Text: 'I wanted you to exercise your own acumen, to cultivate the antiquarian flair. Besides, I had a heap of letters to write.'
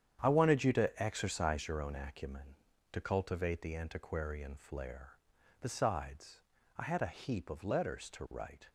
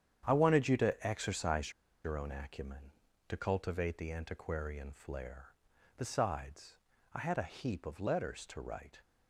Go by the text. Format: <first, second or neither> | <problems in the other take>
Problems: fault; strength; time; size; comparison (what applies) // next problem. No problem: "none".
first | starts louder than the rest; strong; until 1.2 s; 9 dB; strong in the first // pauses between "exercise" and "your"; slight; at 1.7 s; 0.34 s long